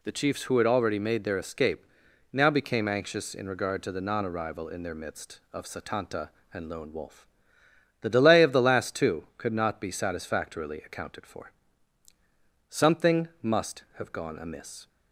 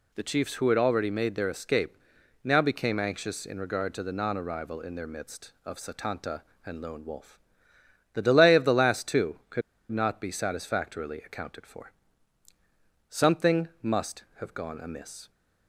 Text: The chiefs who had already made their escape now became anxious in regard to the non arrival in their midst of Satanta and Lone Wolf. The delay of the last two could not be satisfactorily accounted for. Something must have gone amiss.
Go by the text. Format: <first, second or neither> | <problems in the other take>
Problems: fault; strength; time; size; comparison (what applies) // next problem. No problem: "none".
first | pauses between "escape" and "now"; noticeable; at 1.9 s; 0.48 s long; noticeable in the first // pauses between "could" and "not"; slight; at 9.6 s; 0.30 s long